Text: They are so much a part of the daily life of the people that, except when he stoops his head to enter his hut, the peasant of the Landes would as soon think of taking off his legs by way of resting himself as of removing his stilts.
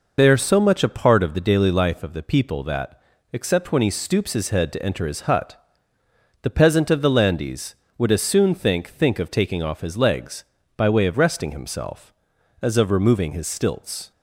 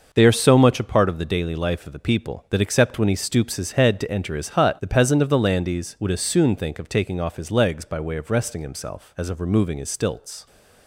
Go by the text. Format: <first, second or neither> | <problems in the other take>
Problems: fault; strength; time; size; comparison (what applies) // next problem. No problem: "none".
second | says "think" twice; at 8.8 s